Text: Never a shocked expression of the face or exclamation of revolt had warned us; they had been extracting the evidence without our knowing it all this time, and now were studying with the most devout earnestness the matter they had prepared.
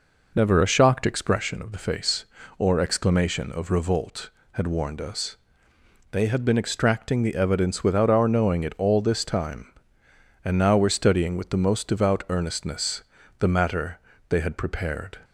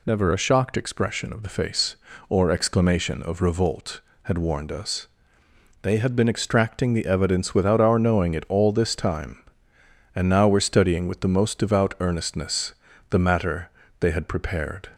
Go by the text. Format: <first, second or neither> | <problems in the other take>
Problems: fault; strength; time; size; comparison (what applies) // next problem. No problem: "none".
second | starts louder than the rest; noticeable; until 1.6 s; 5 dB // pauses between "earnestness" and "the"; at 13.0 s; 0.38 s long; also in the second // pauses between "matter" and "they"; slight; at 13.9 s; 0.30 s long; slight in the second